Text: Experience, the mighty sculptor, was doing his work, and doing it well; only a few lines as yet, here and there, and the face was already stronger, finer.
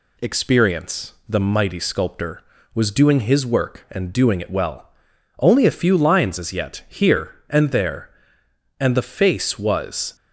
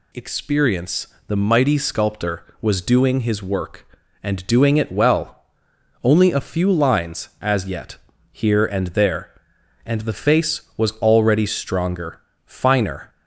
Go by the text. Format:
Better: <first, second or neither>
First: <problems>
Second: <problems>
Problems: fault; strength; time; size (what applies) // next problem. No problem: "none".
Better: second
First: stops before "already stronger finer"; at 10.1 s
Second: none